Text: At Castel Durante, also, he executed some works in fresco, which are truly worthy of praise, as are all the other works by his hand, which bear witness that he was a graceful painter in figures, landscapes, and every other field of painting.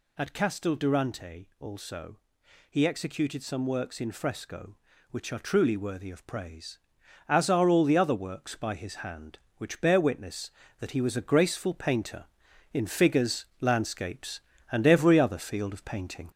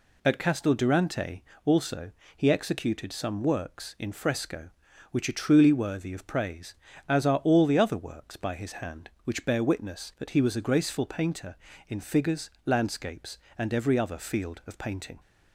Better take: second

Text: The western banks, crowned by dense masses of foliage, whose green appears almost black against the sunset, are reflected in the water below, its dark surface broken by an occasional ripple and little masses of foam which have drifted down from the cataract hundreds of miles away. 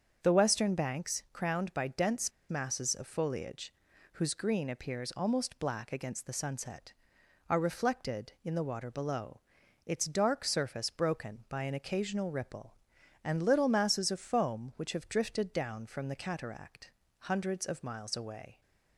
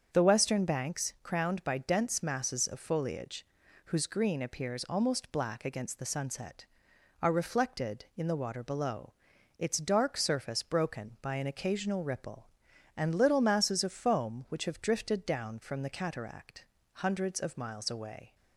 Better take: second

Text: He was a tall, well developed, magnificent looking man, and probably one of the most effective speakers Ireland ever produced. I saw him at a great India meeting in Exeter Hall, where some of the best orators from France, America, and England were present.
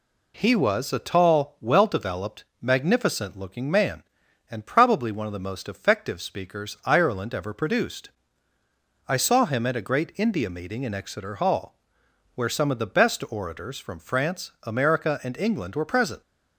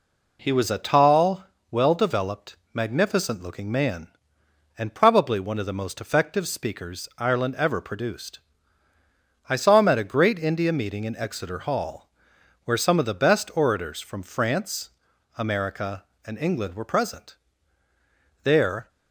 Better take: first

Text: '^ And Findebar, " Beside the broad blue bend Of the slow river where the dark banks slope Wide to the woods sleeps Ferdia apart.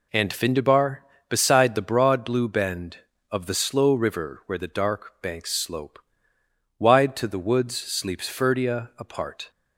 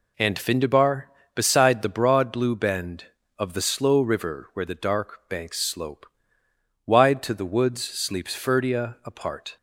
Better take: neither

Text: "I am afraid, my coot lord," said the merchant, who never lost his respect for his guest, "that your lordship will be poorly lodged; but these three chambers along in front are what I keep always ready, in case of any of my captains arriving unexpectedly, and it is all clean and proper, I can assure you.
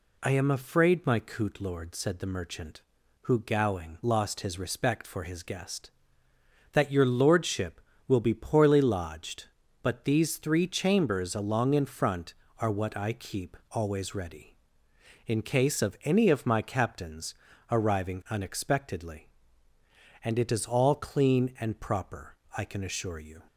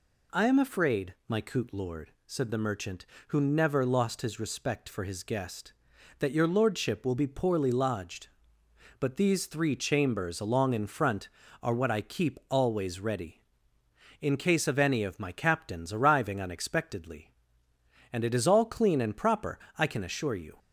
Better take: second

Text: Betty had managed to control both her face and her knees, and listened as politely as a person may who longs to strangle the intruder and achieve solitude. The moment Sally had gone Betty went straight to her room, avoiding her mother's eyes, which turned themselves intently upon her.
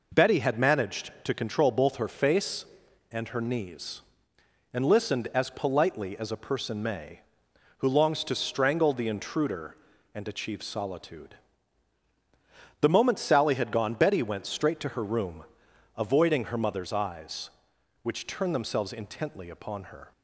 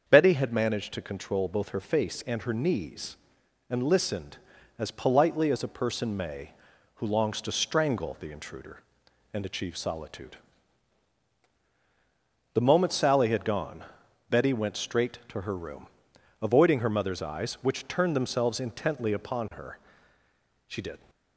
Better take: first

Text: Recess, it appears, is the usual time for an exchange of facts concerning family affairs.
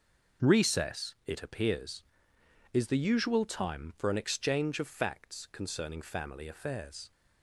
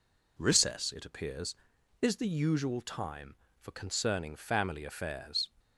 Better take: first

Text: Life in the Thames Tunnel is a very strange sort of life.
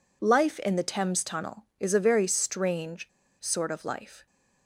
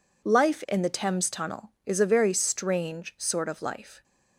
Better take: second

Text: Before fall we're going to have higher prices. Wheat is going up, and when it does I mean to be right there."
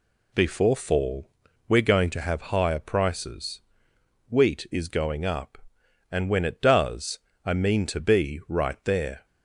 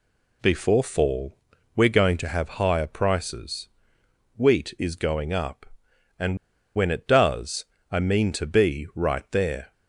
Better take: first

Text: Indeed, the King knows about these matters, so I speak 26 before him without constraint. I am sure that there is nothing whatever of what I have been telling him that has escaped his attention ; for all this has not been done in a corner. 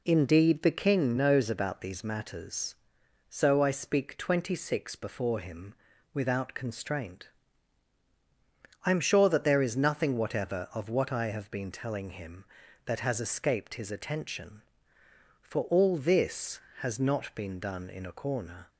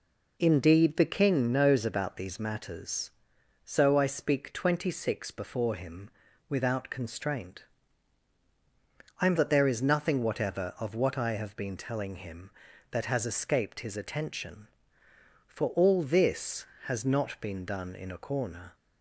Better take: first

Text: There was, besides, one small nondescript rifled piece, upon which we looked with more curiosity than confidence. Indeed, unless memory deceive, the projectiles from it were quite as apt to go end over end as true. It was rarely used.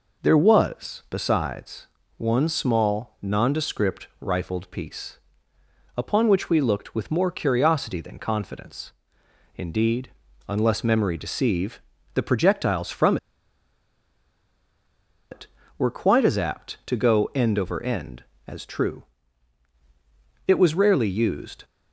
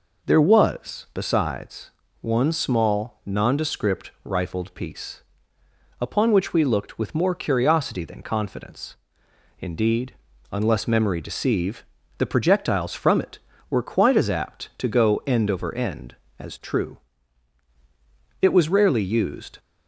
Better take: second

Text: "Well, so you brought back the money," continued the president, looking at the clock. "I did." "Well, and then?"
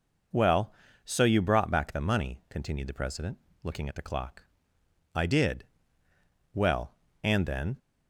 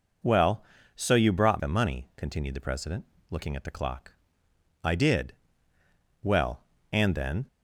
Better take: first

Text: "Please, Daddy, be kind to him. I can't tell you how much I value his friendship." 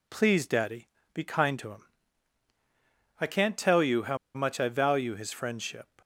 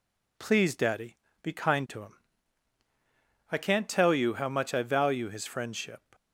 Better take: second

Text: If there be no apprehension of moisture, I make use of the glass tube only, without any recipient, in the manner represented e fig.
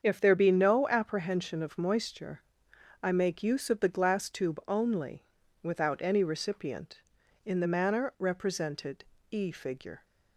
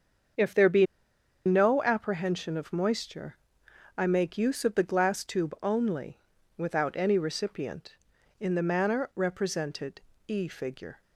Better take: first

